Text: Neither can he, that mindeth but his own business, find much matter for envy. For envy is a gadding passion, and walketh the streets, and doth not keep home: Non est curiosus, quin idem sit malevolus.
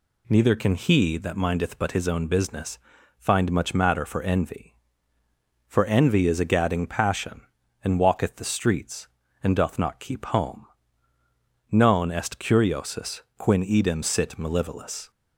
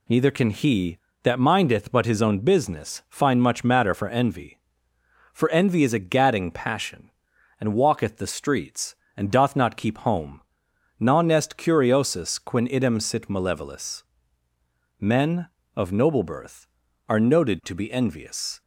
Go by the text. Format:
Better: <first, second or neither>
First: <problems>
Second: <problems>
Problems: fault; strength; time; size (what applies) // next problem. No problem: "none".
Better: first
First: none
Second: goes on to say "Men of noble birth are noted to be envious"; strong; from 15.0 s on; 3.6 s long